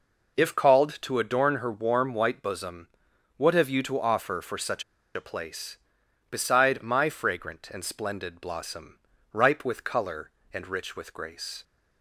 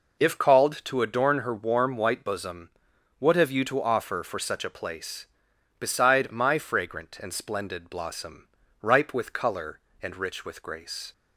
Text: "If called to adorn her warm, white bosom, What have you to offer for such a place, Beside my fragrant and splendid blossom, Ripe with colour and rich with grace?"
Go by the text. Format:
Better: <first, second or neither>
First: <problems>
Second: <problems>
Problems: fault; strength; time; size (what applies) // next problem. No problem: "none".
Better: second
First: pauses between "such" and "a"; slight; at 4.8 s; 0.32 s long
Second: none